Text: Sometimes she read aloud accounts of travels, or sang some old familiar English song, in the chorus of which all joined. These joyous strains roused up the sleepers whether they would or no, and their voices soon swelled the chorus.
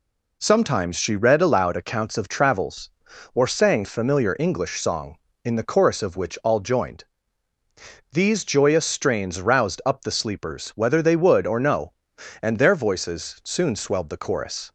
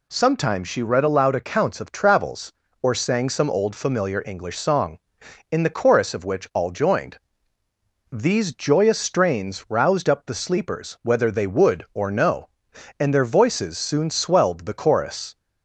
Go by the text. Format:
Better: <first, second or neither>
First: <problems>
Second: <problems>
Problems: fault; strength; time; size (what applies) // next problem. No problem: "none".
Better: second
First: skips "some old"; at 3.8 s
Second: none